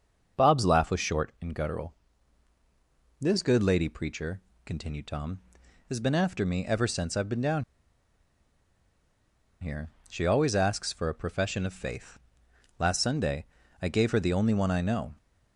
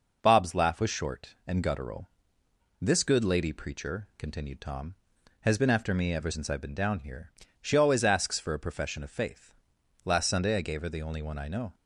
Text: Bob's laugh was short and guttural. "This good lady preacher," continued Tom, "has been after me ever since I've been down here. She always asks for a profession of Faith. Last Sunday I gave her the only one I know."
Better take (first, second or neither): second